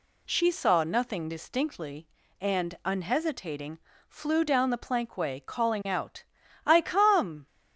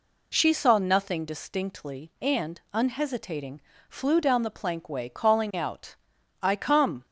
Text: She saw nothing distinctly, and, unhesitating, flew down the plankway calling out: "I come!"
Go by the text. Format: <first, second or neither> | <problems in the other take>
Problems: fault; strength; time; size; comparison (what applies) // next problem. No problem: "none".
neither | none